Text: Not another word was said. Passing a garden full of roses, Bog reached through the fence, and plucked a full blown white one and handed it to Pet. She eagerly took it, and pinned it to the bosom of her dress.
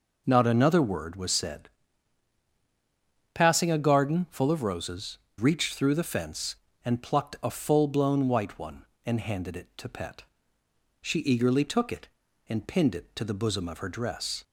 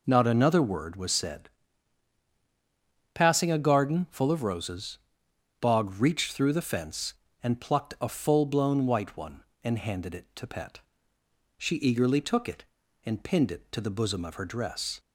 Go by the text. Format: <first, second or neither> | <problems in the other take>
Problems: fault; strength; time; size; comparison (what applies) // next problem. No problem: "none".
second | skips "Bog"; at 5.2 s